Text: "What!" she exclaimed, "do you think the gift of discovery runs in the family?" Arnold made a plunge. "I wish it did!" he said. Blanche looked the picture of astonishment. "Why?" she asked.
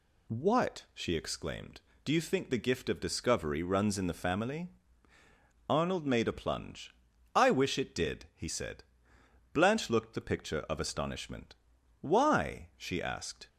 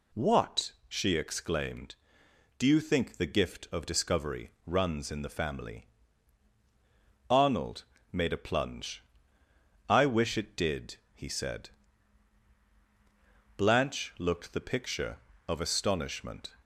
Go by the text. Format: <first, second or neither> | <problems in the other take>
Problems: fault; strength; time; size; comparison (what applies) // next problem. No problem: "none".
first | pauses between "discovery" and "runs"; slight; at 4.5 s; 0.16 s long // pauses between "Arnold" and "made"; slight; at 7.8 s; 0.26 s long // stops before "Why she asked"; at 16.6 s